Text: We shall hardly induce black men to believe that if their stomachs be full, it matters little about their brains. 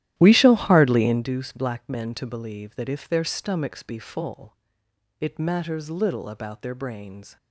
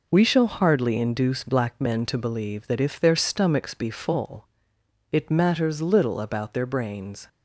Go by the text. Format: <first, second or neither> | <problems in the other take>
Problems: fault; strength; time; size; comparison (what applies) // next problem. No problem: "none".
second | starts louder than the rest; strong; until 1.3 s; 13.5 dB